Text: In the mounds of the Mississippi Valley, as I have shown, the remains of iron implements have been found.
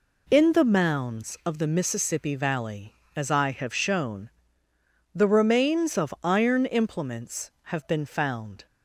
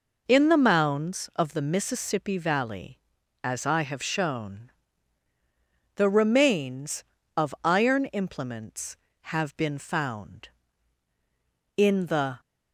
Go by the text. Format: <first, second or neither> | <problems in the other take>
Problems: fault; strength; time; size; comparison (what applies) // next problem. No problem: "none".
first | goes on to say "In the"; noticeable; from 11.7 s on; 0.64 s long